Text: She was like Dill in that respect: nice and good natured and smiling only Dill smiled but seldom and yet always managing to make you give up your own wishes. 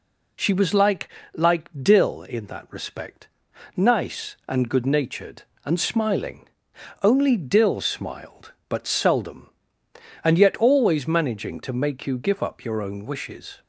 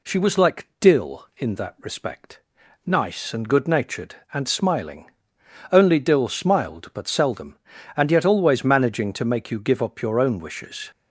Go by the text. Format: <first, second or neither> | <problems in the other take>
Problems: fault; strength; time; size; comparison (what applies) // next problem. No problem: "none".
second | says "like" twice; at 1.3 s // pauses between "smiling" and "only"; noticeable; at 6.4 s; 0.56 s long; noticeable in the second